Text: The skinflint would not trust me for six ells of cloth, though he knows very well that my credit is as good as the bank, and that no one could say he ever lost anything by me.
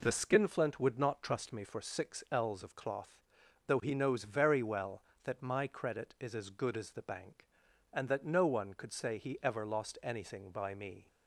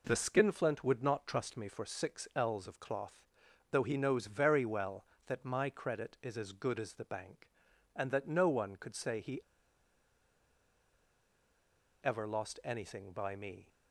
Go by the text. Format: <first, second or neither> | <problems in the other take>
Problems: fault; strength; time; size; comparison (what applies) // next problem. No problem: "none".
first | pauses between "he" and "ever"; strong; at 9.4 s; 2.6 s long